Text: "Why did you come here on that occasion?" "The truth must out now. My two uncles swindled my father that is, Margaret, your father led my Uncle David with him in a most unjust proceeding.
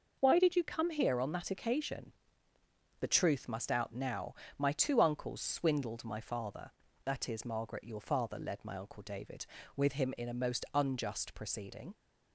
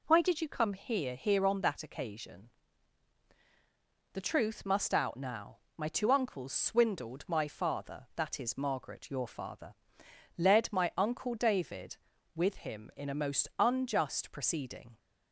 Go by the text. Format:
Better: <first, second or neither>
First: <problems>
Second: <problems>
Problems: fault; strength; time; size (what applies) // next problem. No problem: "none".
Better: first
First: none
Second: says "here" twice; at 1.1 s // pauses between "father" and "led"; noticeable; at 9.7 s; 0.64 s long